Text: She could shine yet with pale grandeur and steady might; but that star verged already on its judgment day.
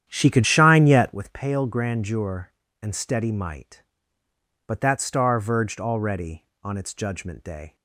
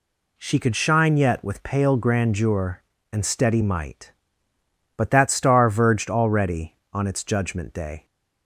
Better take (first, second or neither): second